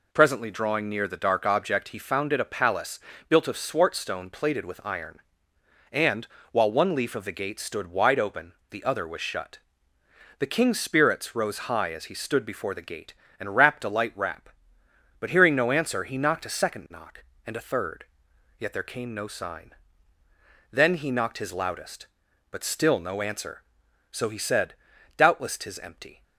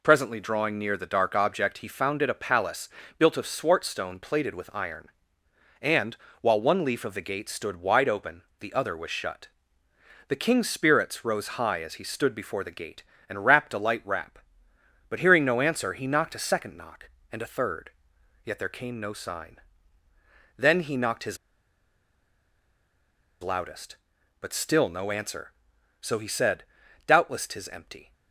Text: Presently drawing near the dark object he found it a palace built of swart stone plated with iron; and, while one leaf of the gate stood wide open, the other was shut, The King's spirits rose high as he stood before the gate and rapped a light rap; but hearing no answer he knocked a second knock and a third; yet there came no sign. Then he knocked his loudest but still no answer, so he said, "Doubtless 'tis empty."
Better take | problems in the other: first | pauses between "palace" and "built"; slight; at 2.8 s; 0.30 s long; slight in the first // pauses between "his" and "loudest"; strong; at 21.3 s; 2.0 s long

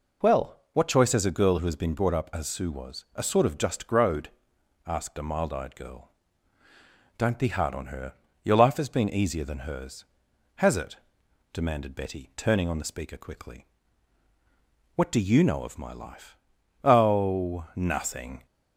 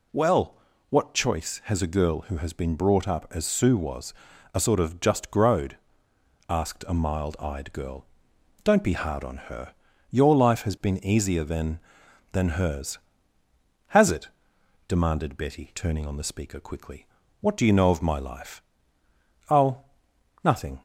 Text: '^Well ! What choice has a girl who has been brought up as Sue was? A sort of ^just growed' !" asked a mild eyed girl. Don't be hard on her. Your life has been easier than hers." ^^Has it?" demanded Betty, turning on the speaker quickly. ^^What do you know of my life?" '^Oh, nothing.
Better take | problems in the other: first | says "than" twice; at 12.3 s

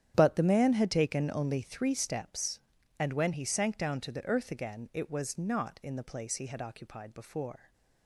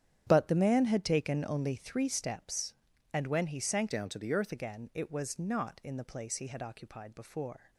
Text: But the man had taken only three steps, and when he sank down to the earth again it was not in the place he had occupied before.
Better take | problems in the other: first | starts louder than the rest; strong; until 1.2 s; 9.5 dB; strong in the first // changes voice from "down" to "earth"; from 3.9 to 4.5 s; 0.6 s long

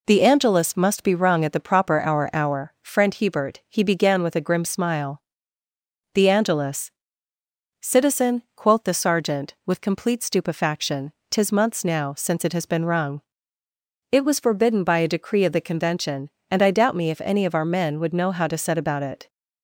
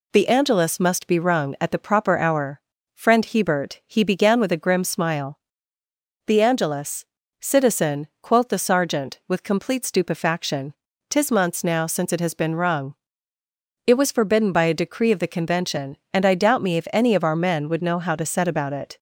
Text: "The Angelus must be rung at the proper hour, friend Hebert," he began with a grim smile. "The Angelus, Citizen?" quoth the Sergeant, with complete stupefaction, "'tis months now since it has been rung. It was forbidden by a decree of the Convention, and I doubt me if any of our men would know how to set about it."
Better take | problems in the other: second | says "hour" twice; at 2.3 s

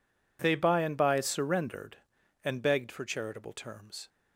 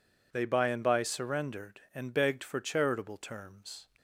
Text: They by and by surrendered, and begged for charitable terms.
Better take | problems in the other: neither | none

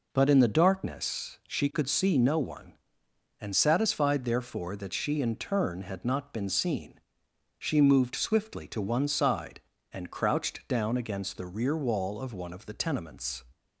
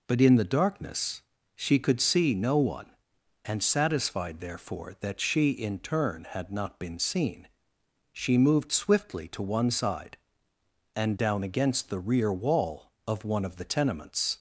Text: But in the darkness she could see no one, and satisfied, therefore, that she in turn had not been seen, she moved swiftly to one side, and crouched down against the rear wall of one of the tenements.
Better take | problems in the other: first | pauses between "darkness" and "she"; slight; at 1.2 s; 0.32 s long // skips "crouched"; at 11.1 s

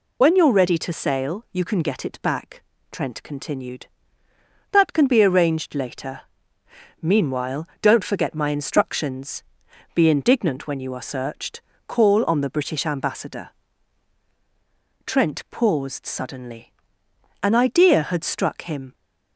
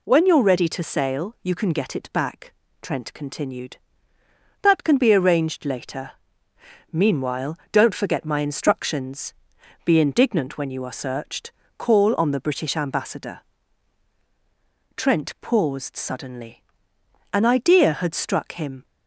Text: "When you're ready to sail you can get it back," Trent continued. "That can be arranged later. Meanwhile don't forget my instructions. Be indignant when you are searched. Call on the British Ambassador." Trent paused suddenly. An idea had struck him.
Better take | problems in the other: second | loses the start of "When"; at 0.2 s; 45 ms // pauses between "Meanwhile" and "don't"; slight; at 7.6 s; 0.16 s long; slight in the second

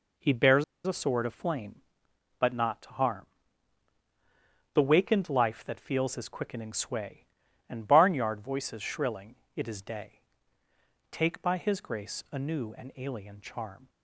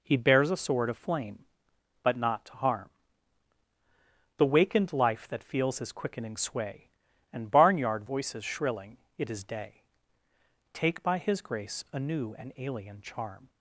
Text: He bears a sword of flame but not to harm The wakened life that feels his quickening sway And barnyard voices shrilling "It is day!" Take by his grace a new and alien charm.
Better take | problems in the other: second | pauses between "bears" and "a"; slight; at 0.6 s; 0.22 s long // pauses between "harm" and "The"; strong; at 3.2 s; 1.5 s long; strong in the second // pauses between "shrilling" and "It"; slight; at 9.3 s; 0.18 s long; slight in the second

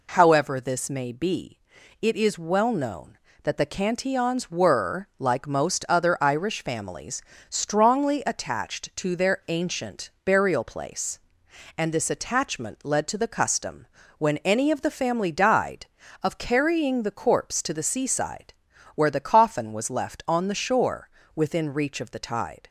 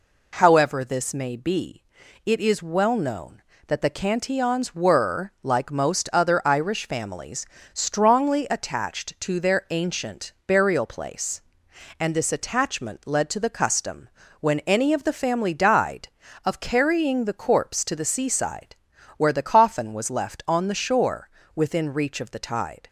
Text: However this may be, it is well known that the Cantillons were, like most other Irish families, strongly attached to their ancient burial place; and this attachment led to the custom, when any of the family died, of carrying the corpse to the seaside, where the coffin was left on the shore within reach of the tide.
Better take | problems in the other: neither | pauses between "ancient" and "burial"; slight; the same in both // pauses between "shore" and "within"; slight; the same in both

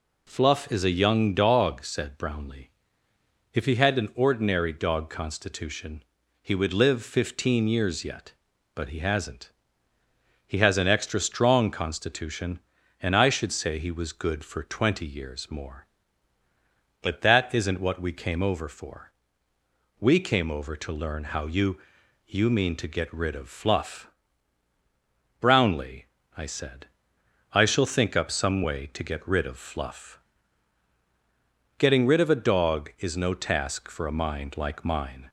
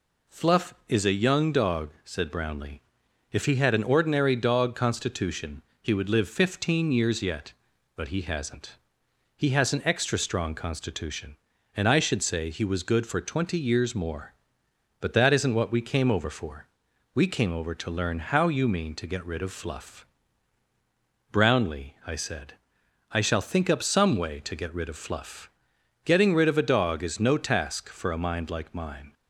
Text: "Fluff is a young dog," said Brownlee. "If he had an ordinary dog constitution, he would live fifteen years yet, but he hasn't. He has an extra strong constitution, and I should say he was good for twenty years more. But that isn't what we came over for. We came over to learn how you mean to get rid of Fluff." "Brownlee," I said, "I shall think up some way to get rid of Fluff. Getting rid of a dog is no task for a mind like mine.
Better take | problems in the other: second | says "you" twice; at 22.2 s

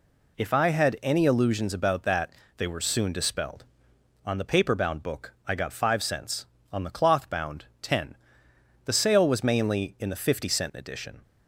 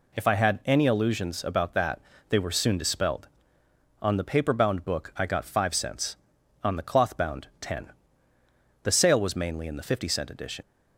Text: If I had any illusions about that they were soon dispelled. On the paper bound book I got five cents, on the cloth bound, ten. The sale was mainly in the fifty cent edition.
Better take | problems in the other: first | pauses between "that" and "they"; slight; at 1.9 s; 0.30 s long; slight in the first // leaves "edition" unfinished; at 10.6 s; 95 ms

